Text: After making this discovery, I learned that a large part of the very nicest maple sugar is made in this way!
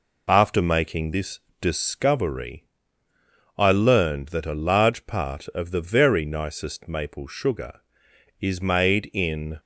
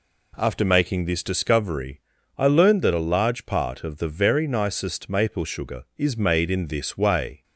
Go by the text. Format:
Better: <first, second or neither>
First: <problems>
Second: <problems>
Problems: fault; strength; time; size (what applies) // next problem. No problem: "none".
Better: second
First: pauses between "this" and "discovery"; slight; at 1.3 s; 0.22 s long // stops before "this way"; at 9.5 s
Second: none